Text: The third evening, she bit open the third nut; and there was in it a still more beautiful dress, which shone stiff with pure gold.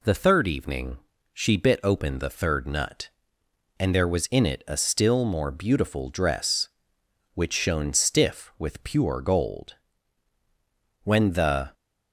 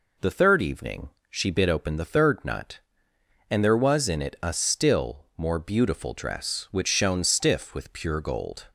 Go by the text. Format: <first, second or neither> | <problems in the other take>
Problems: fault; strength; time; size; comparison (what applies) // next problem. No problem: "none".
second | goes on to say "When the"; noticeable; from 11.0 s on; 0.70 s long